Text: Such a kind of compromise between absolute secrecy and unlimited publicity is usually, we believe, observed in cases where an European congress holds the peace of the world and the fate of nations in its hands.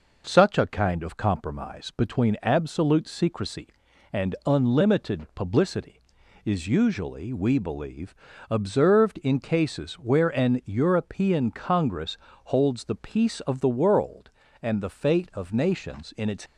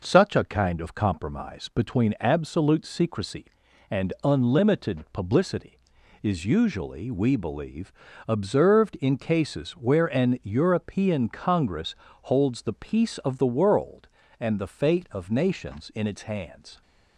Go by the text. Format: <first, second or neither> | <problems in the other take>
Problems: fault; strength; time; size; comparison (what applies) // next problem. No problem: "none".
second | pauses between "congress" and "holds"; slight; at 12.1 s; 0.28 s long; slight in the second // stops before "hands"; at 16.4 s